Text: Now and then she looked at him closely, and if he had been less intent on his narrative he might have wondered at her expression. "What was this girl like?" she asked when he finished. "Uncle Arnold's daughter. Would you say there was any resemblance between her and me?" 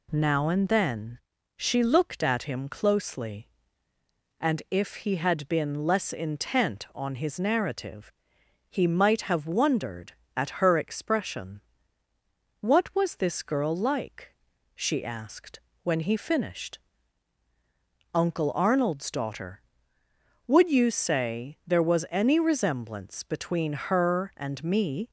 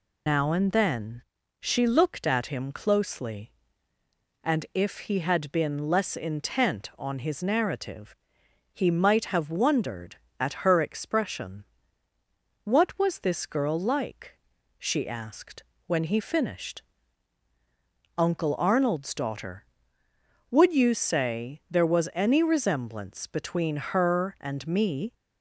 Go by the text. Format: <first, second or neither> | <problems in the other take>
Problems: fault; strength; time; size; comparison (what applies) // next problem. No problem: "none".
first | loses the start of "Now"; at 0.2 s; 140 ms // pauses between "then" and "she"; slight; at 1.2 s; 0.36 s long; slight in the first // pauses between "narrative" and "he"; noticeable; at 8.1 s; 0.60 s long; noticeable in the first // pauses between "asked" and "when"; slight; at 15.6 s; 0.24 s long; slight in the first